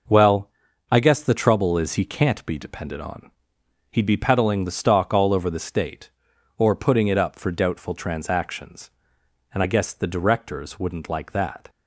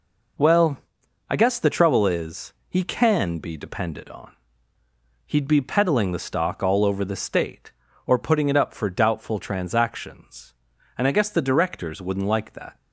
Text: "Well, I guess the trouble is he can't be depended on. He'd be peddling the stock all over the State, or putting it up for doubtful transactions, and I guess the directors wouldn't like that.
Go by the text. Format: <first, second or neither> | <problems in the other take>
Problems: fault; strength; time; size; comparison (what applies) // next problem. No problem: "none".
first | pauses between "is" and "he"; slight; at 2.5 s; 0.16 s long // says "can" for "can't"; at 2.8 s